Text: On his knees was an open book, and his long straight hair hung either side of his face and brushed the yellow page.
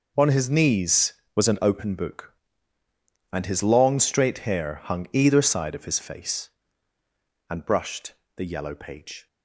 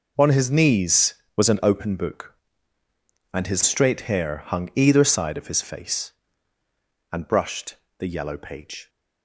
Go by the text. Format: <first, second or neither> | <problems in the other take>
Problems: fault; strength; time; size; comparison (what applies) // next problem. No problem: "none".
first | skips "long"; at 3.6 s // pauses between "brushed" and "the"; slight; at 7.7 s; 0.24 s long; slight in the first